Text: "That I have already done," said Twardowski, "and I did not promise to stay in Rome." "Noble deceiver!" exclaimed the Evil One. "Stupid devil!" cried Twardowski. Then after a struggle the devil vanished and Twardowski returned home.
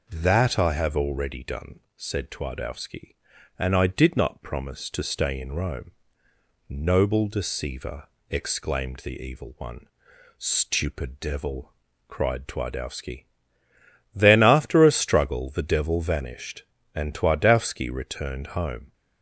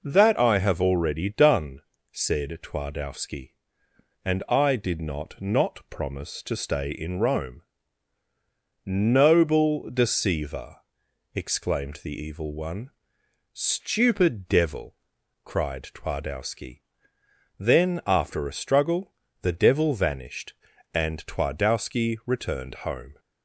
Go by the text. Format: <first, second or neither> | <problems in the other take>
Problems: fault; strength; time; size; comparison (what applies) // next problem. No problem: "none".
first | says "not" twice; at 5.3 s // pauses between "struggle" and "the"; slight; at 19.1 s; 0.30 s long // pauses between "returned" and "home"; slight; at 22.7 s; 0.16 s long